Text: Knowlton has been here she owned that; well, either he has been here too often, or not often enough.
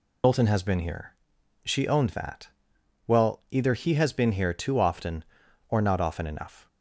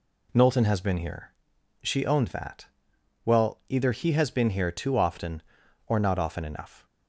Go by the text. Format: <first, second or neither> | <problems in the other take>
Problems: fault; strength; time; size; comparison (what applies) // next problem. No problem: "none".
second | loses the start of "Knowlton"; at 0.2 s; 110 ms // pauses between "here" and "she"; noticeable; at 1.1 s; 0.50 s long; noticeable in the second